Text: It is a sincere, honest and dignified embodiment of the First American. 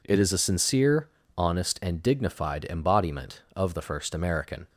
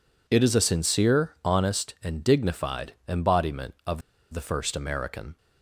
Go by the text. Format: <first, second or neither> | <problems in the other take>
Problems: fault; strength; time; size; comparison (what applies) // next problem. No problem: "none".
first | pauses between "of" and "the"; slight; at 4.0 s; 0.31 s long